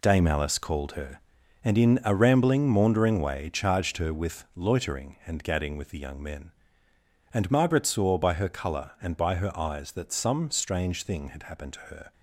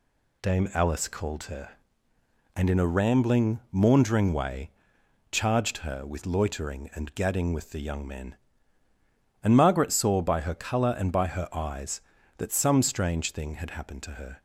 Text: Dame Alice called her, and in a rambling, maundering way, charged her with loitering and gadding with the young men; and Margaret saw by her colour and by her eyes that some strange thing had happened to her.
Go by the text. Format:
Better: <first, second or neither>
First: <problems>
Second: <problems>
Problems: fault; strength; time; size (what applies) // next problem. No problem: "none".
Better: second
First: gets quieter; strong; throughout; 9 dB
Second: none